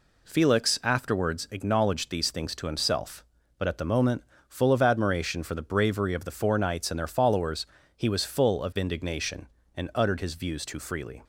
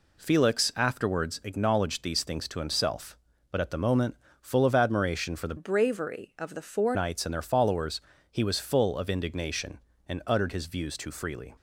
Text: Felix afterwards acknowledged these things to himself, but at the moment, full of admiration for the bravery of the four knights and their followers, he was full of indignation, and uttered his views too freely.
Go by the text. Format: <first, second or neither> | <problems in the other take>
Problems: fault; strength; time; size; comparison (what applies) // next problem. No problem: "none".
first | changes voice from "bravery" to "four"; from 5.5 to 6.9 s; 1.4 s long